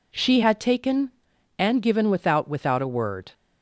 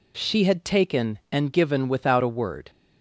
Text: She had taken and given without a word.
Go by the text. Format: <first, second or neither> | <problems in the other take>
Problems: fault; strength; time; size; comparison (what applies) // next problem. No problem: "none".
second | says "without" twice; at 2.4 s